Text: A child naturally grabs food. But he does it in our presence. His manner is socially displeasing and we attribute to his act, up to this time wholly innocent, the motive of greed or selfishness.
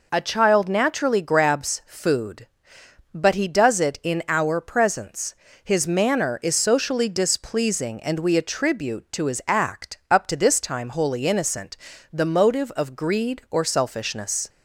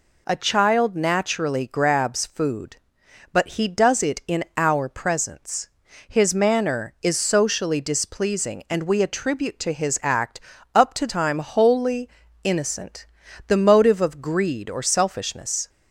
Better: first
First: none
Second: skips "this"; at 11.0 s // pauses between "wholly" and "innocent"; slight; at 12.0 s; 0.34 s long

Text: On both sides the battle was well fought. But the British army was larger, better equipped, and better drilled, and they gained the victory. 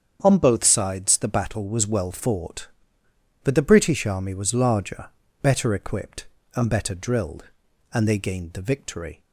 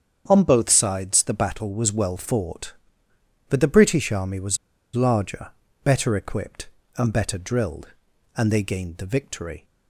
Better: first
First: starts louder than the rest; strong; until 1.2 s; 8 dB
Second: starts louder than the rest; strong; until 1.2 s; 8 dB // pauses between "was" and "larger"; at 4.5 s; 0.37 s long

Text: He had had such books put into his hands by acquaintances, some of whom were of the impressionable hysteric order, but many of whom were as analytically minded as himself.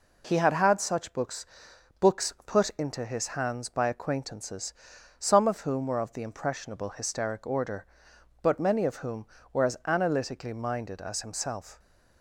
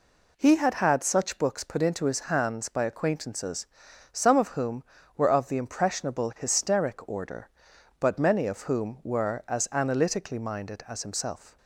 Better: second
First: says "books" twice; at 1.9 s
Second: none

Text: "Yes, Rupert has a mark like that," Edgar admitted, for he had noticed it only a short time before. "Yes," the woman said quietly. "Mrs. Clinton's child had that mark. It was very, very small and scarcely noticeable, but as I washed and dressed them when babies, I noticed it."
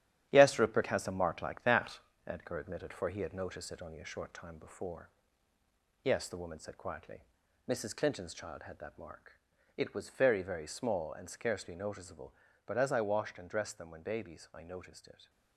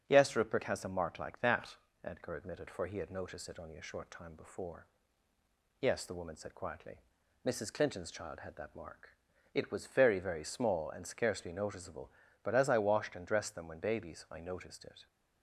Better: second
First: gets quieter; throughout; 7 dB // starts louder than the rest; strong; until 1.3 s; 11 dB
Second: starts louder than the rest; strong; until 1.0 s; 7.5 dB

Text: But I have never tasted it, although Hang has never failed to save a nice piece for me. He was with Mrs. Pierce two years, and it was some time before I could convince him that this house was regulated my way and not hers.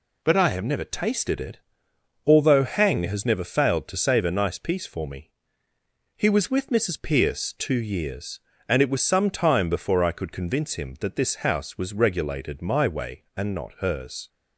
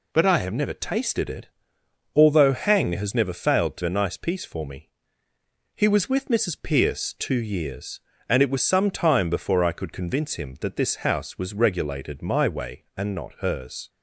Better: first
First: none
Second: skips "save"; at 3.8 s

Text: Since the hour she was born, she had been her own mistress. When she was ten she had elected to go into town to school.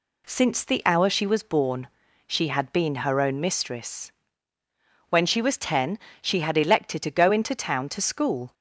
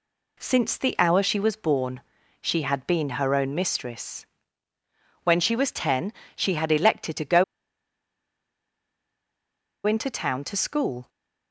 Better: first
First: pauses between "ten" and "she"; slight; at 5.9 s; 0.24 s long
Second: pauses between "ten" and "she"; slight; at 6.1 s; 0.24 s long // pauses between "go" and "into"; strong; at 7.4 s; 2.4 s long

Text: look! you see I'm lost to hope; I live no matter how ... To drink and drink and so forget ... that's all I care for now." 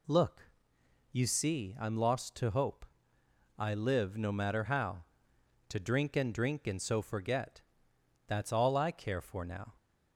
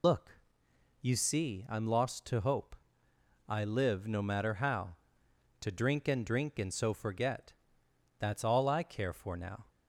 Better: first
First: none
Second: loses the start of "look"; at 0.0 s; 80 ms

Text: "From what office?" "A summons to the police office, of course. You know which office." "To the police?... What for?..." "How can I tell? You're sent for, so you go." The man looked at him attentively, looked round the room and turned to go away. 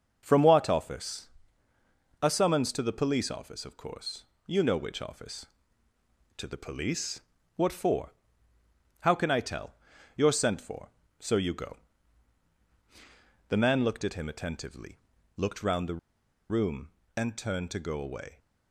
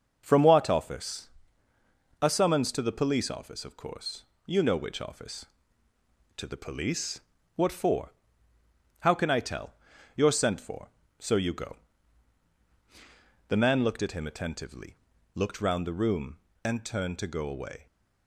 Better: second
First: pauses between "the" and "room"; noticeable; at 15.9 s; 0.53 s long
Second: none

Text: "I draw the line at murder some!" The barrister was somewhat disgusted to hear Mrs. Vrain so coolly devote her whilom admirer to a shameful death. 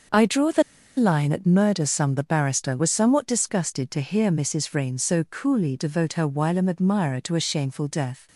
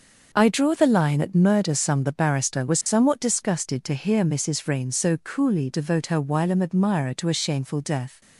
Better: second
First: starts louder than the rest; until 1.4 s; 6 dB // pauses between "the" and "line"; slight; at 0.6 s; 0.34 s long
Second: starts louder than the rest; until 1.3 s; 6 dB

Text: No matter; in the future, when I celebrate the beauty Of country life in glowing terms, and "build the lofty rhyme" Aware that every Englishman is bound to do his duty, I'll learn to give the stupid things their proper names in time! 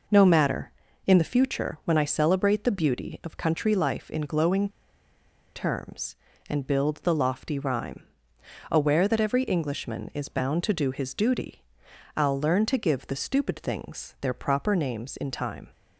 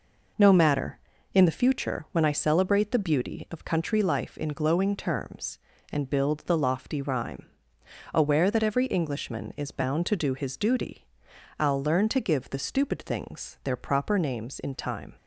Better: second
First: pauses between "glowing" and "terms"; noticeable; at 4.6 s; 0.86 s long // pauses between "rhyme" and "Aware"; noticeable; at 8.0 s; 0.66 s long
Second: pauses between "rhyme" and "Aware"; noticeable; at 7.4 s; 0.66 s long

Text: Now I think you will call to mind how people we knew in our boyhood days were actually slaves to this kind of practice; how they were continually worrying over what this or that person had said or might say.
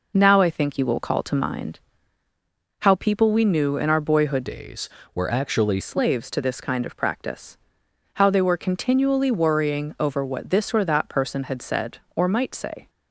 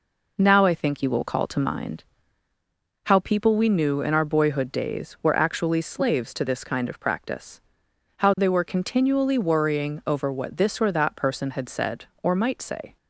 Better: second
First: pauses between "mind" and "how"; at 1.8 s; 1.0 s long // changes voice from "days" to "actually"; from 4.4 to 5.8 s; 1.4 s long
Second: pauses between "mind" and "how"; at 2.0 s; 1.0 s long

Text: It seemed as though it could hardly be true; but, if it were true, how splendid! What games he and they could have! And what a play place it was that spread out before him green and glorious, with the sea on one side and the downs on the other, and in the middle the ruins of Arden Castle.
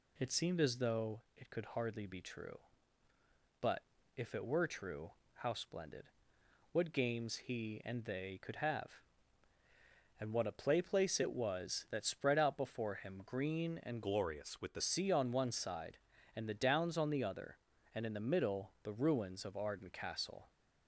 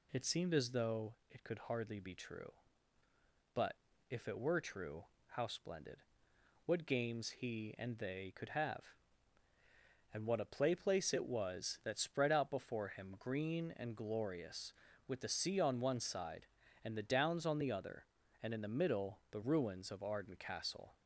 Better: second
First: pauses between "though" and "it"; slight; at 1.2 s; 0.16 s long // changes voice from "glorious" to "the"; from 14.0 to 14.8 s; 0.8 s long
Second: pauses between "though" and "it"; slight; at 1.1 s; 0.16 s long

